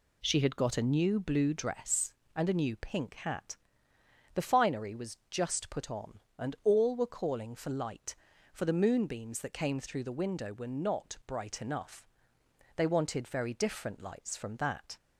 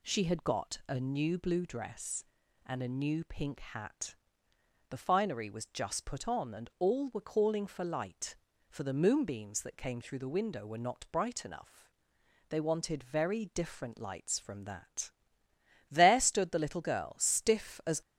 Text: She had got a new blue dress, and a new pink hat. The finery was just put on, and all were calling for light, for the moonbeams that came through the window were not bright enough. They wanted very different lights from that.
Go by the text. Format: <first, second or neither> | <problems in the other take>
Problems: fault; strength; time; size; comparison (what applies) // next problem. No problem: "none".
first | goes on to say "There stood the little girl stiff as"; strong; from 15.8 s on; 2.1 s long